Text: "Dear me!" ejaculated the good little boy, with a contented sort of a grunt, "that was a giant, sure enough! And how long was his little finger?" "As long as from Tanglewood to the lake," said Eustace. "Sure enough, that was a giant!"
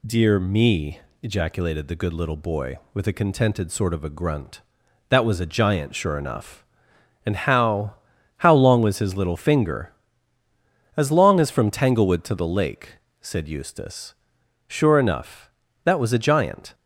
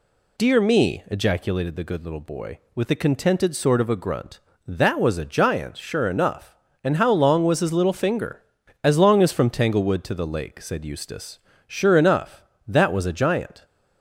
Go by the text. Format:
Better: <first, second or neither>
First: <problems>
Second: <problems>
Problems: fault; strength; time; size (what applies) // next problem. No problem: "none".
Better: second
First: says "how" twice; at 8.3 s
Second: none